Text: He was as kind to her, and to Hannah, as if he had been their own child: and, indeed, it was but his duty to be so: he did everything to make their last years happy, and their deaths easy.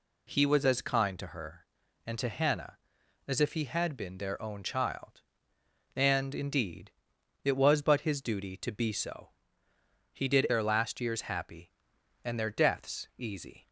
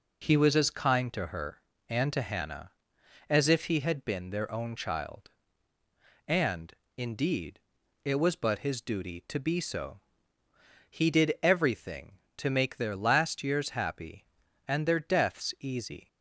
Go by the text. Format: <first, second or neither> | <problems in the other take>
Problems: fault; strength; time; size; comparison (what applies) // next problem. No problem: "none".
second | skips "everything to make"; at 10.4 s